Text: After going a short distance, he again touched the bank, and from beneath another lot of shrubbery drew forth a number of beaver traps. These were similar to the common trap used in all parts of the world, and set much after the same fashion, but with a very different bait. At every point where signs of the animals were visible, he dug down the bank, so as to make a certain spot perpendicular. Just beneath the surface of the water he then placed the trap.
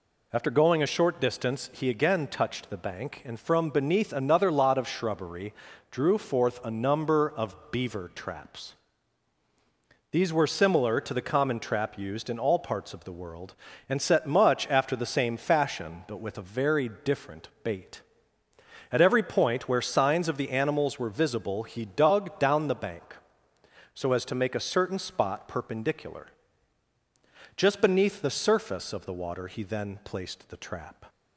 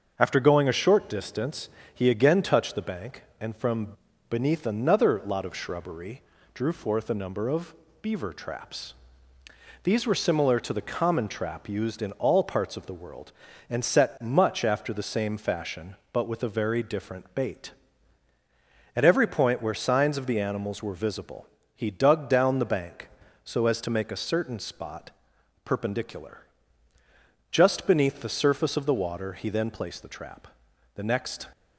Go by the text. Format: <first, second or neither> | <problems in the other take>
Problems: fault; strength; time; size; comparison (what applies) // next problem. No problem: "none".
first | starts louder than the rest; until 1.1 s; 6.5 dB // pauses between "from" and "beneath"; slight; at 3.9 s; 0.34 s long // pauses between "shrubbery" and "drew"; slight; at 6.2 s; 0.32 s long; slight in the first // pauses between "of" and "beaver"; slight; at 7.7 s; 0.28 s long // pauses between "spot" and "perpendicular"; noticeable; at 25.1 s; 0.54 s long // goes on to say "The next"; from 30.9 s on; 0.50 s long